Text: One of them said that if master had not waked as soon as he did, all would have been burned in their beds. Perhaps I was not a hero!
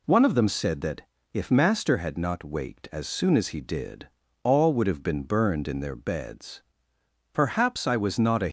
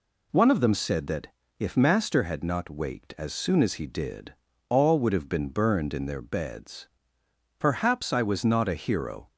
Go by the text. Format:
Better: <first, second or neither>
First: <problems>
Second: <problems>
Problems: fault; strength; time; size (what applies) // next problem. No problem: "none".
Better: second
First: pauses between "that" and "if"; slight; at 1.0 s; 0.32 s long // stops before "hero"; at 8.4 s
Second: pauses between "that" and "if"; slight; at 1.2 s; 0.32 s long